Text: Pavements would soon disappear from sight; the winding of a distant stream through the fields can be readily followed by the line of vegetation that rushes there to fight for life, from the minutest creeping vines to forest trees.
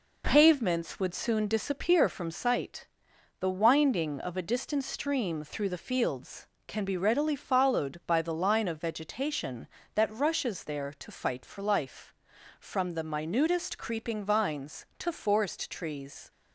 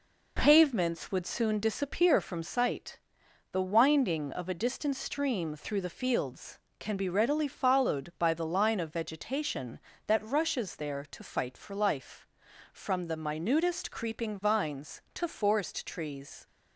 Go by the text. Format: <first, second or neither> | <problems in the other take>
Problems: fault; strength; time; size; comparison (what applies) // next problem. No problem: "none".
neither | none